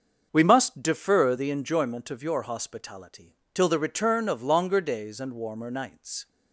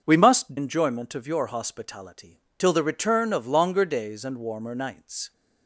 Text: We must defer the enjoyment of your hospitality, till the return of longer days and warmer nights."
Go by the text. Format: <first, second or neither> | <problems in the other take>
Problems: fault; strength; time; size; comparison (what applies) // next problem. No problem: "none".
first | starts louder than the rest; until 1.0 s; 6.5 dB; also in the first // skips "defer the"; at 0.5 s